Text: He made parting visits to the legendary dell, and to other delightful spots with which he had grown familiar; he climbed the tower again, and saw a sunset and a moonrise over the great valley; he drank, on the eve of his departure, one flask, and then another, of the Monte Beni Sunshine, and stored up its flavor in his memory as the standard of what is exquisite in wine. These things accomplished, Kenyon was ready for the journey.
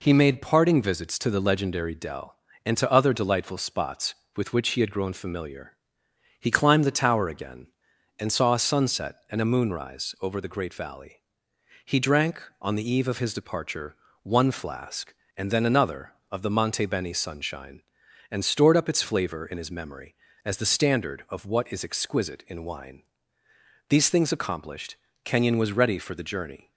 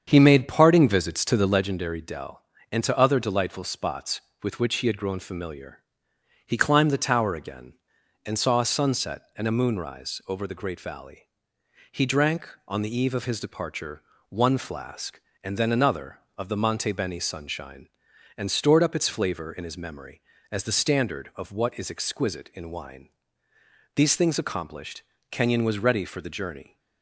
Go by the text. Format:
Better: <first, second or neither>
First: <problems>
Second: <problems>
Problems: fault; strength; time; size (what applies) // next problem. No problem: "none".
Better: first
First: none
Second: starts louder than the rest; strong; until 1.6 s; 7.5 dB